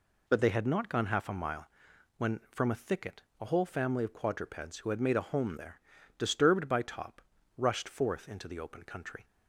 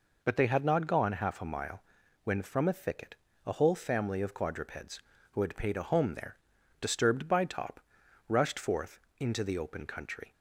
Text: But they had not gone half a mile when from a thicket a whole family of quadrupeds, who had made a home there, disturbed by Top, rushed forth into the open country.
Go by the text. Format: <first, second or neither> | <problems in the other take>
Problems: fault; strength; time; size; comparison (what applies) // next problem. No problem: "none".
first | pauses between "mile" and "when"; at 1.8 s; 0.42 s long; noticeable in the first // pauses between "thicket" and "a"; slight; at 3.1 s; 0.30 s long; slight in the first // says "paid" for "made"; at 5.5 s // pauses between "forth" and "into"; slight; at 8.9 s; 0.18 s long